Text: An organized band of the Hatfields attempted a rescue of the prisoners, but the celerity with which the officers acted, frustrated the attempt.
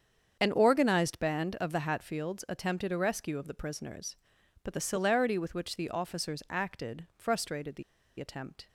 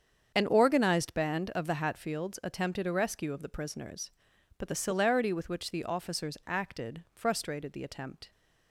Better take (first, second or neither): second